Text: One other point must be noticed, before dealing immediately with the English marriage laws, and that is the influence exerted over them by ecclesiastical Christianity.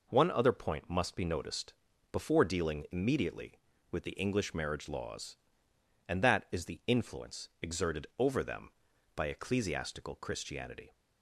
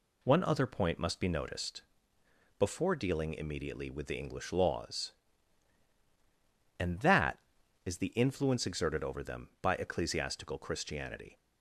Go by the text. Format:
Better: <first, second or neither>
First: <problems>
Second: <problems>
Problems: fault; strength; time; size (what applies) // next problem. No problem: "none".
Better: first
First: none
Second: skips "marriage"; at 4.5 s